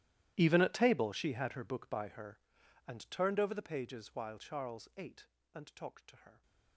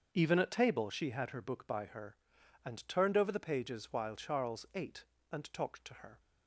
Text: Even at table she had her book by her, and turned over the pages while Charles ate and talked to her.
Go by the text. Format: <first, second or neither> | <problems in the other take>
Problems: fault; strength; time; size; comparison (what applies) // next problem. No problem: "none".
second | gets quieter; strong; throughout; 21.5 dB // starts louder than the rest; strong; until 1.3 s; 13.5 dB; also in the second